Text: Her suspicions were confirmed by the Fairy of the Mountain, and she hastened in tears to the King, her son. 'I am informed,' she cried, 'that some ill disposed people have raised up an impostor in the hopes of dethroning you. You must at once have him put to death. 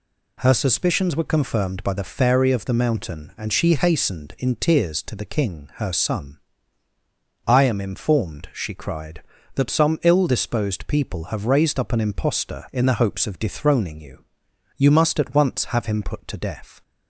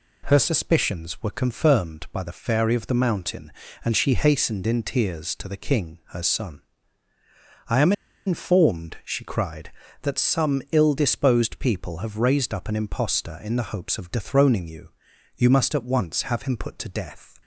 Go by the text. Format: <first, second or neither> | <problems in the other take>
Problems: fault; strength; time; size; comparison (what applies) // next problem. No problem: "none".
first | pauses between "am" and "informed"; slight; at 7.9 s; 0.34 s long